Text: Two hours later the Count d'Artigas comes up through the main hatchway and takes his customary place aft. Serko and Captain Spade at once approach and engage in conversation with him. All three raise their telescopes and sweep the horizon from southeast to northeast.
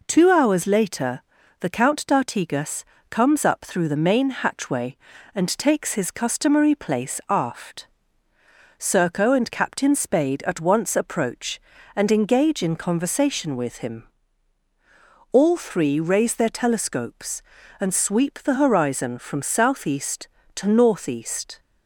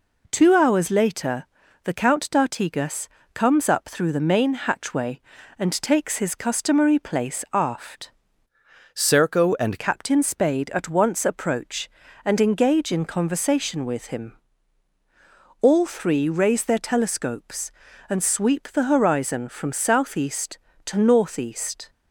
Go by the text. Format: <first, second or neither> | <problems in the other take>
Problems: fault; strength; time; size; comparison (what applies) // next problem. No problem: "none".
first | pauses between "later" and "the"; at 1.4 s; 0.38 s long; also in the first // pauses between "d'Artigas" and "comes"; slight; at 3.0 s; 0.26 s long; slight in the first // changes voice from "Serko" to "and"; from 8.9 to 9.7 s; 0.8 s long